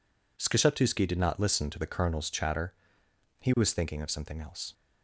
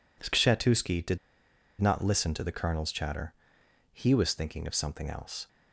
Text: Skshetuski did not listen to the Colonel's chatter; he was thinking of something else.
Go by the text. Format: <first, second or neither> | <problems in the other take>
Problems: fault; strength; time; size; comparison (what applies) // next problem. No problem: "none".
first | pauses between "did" and "not"; noticeable; at 1.1 s; 0.63 s long